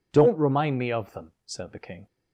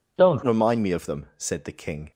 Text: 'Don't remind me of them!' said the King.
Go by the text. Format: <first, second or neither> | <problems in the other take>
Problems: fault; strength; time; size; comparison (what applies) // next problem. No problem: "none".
first | changes voice at "remind"; from 0.4 s on; 1.7 s long